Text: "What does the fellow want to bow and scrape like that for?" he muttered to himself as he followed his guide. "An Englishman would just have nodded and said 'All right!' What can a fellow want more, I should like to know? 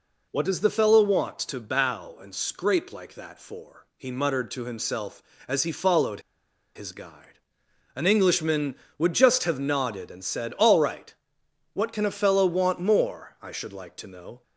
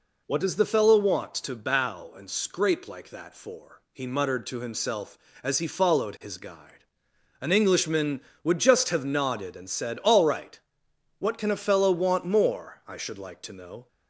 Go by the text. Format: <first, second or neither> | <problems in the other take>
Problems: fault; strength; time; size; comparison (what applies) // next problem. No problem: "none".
second | pauses between "followed" and "his"; noticeable; at 6.2 s; 0.55 s long